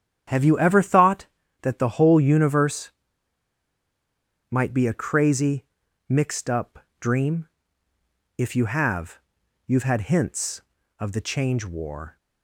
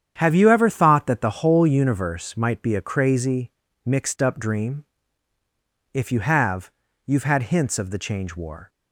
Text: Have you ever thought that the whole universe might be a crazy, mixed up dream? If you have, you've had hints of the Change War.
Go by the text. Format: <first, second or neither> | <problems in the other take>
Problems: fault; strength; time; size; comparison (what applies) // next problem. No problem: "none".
second | starts louder than the rest; strong; until 1.7 s; 9.5 dB; strong in the second // pauses between "universe" and "might"; strong; at 2.9 s; 1.5 s long // pauses between "up" and "dream"; slight; at 6.7 s; 0.22 s long